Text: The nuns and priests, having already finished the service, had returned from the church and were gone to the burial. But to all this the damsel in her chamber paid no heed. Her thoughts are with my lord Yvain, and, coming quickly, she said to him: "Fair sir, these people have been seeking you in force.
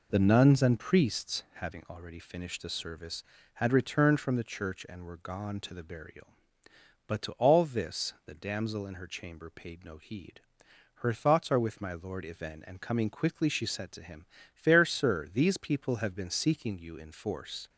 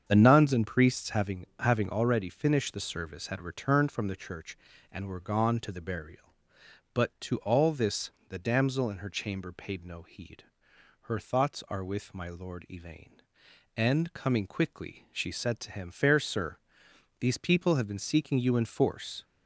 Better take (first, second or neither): first